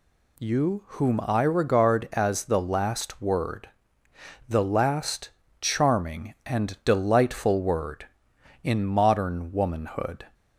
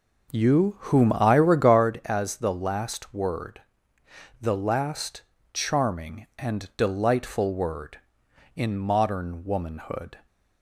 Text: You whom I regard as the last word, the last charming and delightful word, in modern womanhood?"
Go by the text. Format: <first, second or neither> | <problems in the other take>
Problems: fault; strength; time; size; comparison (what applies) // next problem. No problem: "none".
first | starts louder than the rest; noticeable; until 1.9 s; 5.5 dB // pauses between "last" and "charming"; slight; at 5.2 s; 0.32 s long; slight in the first